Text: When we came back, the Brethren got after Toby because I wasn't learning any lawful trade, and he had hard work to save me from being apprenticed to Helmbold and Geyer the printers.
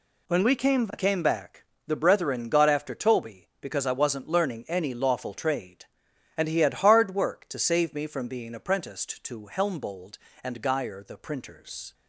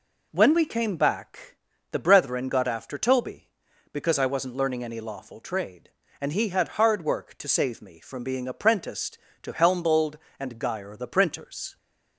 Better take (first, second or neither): second